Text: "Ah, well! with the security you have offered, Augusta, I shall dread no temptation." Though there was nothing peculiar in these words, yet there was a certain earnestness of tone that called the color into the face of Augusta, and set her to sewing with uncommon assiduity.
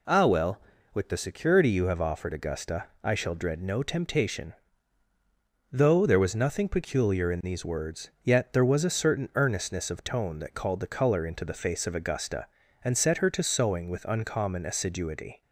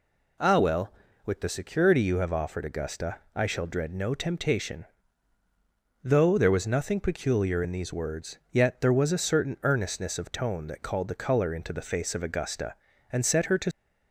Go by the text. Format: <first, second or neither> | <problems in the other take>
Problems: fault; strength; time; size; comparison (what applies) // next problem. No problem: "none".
first | stops before "sewing with uncommon assiduity"; at 13.7 s